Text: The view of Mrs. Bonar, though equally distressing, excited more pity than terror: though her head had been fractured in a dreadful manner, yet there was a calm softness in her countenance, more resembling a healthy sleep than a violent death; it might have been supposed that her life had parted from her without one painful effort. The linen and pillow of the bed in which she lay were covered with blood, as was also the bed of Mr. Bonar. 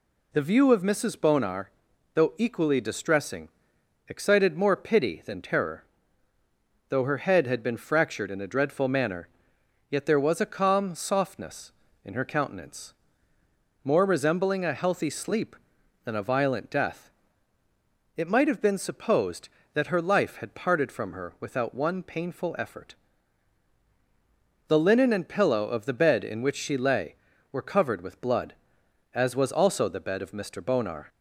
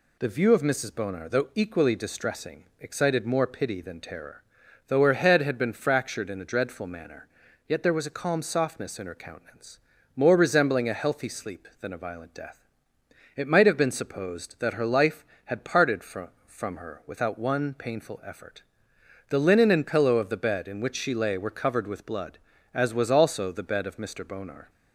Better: first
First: none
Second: says "from" twice; at 16.4 s

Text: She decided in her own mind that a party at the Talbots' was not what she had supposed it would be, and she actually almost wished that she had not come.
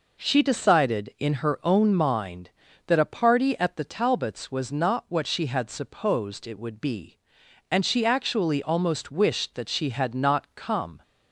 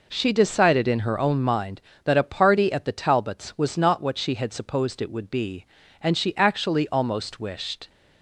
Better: first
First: none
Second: stops before "that she had not come"; at 7.8 s

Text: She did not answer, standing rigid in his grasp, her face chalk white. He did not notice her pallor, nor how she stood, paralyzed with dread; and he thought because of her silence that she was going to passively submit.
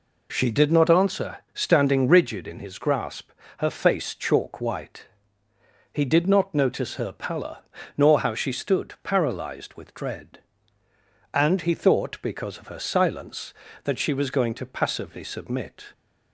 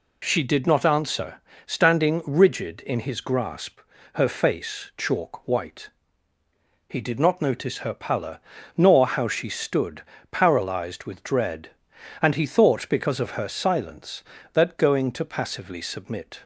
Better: first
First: none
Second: skips "she was"; at 14.7 s

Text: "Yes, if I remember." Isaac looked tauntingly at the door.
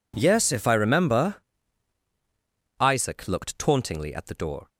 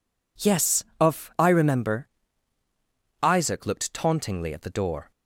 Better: first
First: none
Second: says "of" for "if"; at 1.0 s

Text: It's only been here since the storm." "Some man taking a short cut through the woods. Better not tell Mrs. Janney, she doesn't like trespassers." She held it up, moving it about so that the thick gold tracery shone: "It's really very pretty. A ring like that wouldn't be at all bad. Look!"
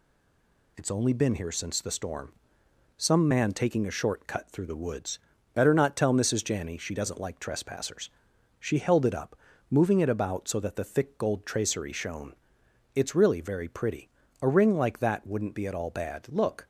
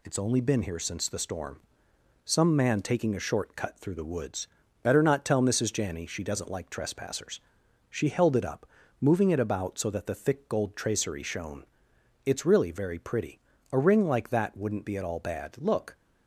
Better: second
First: stays silent before the first word; slight; until 0.7 s; 0.7 s long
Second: none

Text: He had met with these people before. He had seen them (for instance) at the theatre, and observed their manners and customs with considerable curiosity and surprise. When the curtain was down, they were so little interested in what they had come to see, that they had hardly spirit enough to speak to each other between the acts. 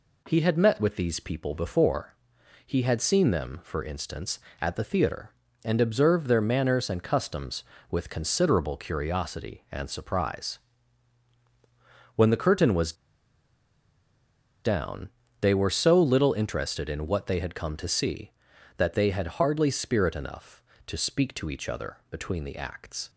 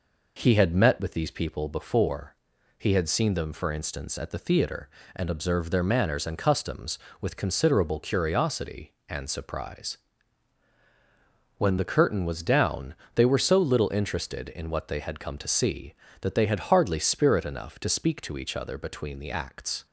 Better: second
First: pauses between "was" and "down"; strong; at 12.9 s; 1.7 s long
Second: none

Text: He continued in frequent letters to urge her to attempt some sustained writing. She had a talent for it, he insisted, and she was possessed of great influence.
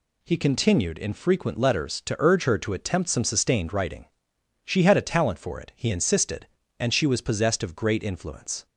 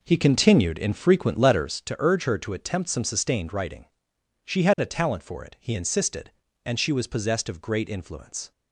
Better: first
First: none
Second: starts louder than the rest; noticeable; until 1.9 s; 4.5 dB

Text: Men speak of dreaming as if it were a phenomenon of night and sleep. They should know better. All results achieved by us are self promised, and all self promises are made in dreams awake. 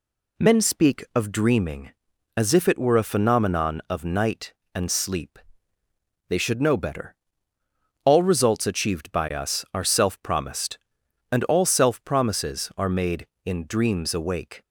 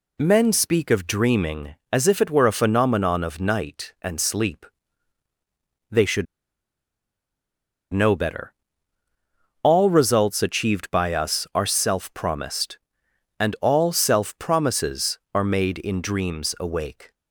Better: first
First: none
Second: pauses between "should" and "know"; strong; at 6.2 s; 1.6 s long

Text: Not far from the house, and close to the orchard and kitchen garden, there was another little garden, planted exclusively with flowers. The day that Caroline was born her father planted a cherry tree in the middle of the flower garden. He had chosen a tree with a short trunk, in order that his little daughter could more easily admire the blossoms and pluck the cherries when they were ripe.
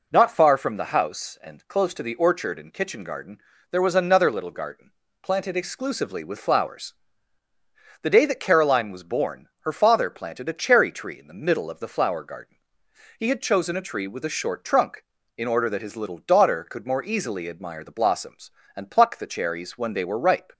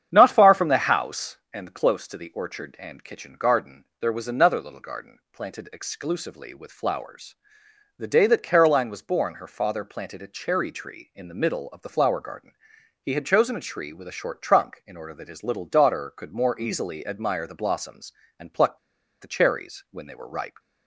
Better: first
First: none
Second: starts louder than the rest; strong; until 1.1 s; 8.5 dB // pauses between "pluck" and "the"; at 18.7 s; 0.44 s long

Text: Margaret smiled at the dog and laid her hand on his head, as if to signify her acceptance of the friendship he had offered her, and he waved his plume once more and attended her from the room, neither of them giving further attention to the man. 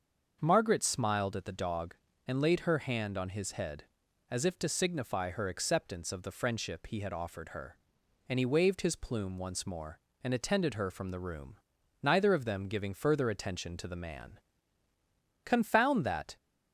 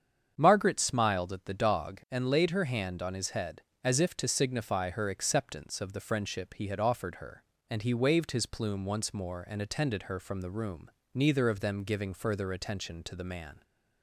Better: second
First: starts louder than the rest; until 1.4 s; 6.5 dB // goes on to say "Confound that"; noticeable; from 15.4 s on; 0.92 s long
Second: starts louder than the rest; strong; until 1.3 s; 8 dB

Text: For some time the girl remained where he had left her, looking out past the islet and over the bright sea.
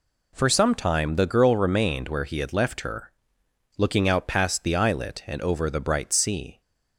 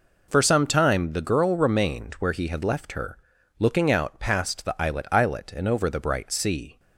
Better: first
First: none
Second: says "islet" twice; at 5.1 s

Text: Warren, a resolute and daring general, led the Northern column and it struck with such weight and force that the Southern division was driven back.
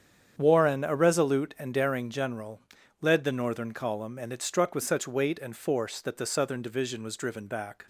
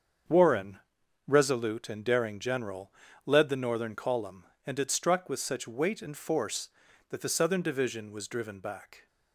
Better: first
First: starts louder than the rest; strong; until 1.3 s; 8 dB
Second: starts louder than the rest; strong; until 1.7 s; 7 dB // skips "a"; at 1.0 s

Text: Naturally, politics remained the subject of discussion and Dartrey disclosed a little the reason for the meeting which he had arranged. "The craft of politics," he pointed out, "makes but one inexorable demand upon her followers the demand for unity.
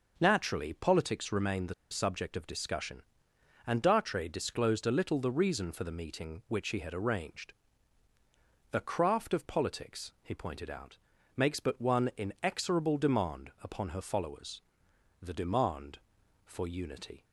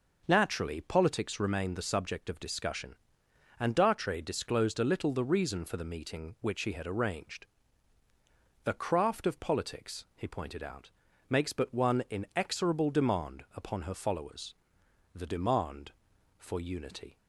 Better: second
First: pauses between "the" and "subject"; slight; at 1.7 s; 0.17 s long // pauses between "followers" and "the"; noticeable; at 14.5 s; 0.62 s long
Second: pauses between "followers" and "the"; noticeable; at 14.5 s; 0.62 s long

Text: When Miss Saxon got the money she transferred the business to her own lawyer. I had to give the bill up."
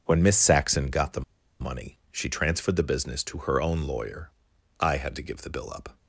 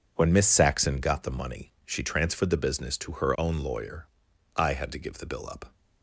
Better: second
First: pauses between "the" and "money"; at 1.2 s; 0.38 s long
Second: none

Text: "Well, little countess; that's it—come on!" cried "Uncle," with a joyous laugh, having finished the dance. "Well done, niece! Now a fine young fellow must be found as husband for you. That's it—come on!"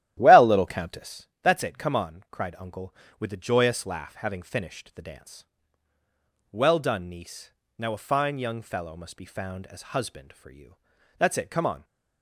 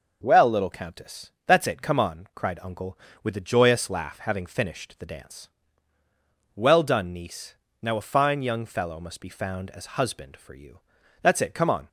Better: second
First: starts louder than the rest; strong; until 1.2 s; 12.5 dB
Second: none

